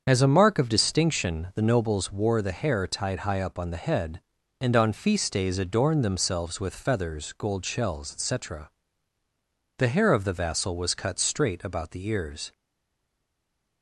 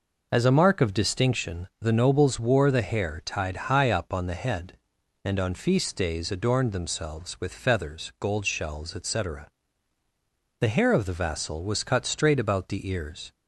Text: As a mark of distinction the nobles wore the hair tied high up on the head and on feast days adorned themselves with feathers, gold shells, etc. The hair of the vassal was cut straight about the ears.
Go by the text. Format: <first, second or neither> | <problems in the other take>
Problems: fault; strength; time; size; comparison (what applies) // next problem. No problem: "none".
second | starts louder than the rest; strong; until 1.0 s; 7 dB // stays silent after the last word; noticeable; from 12.5 s on; 1.3 s long